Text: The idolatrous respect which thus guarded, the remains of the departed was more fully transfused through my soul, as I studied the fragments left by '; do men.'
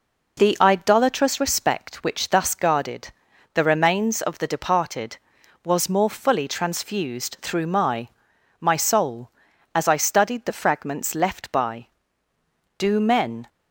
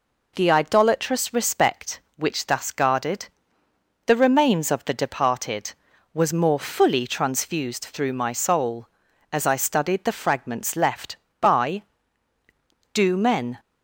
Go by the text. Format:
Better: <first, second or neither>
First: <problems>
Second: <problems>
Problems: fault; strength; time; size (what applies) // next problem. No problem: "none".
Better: second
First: says "my" twice; at 8.6 s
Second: none